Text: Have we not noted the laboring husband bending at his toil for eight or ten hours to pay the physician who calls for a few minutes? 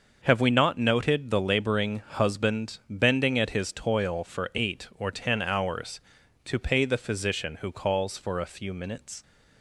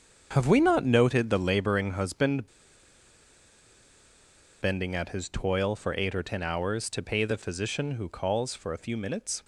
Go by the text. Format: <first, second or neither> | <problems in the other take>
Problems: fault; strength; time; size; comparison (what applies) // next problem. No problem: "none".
first | starts louder than the rest; until 1.3 s; 7 dB; noticeable in the first // pauses between "husband" and "bending"; strong; at 2.4 s; 2.1 s long